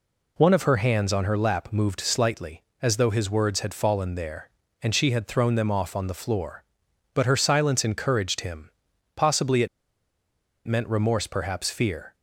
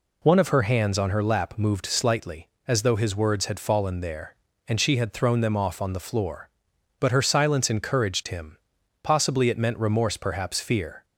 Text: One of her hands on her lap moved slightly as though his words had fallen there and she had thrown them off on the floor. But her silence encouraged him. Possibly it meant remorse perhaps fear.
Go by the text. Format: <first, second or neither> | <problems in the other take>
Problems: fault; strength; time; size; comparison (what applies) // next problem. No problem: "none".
second | pauses between "it" and "meant"; at 9.6 s; 1.0 s long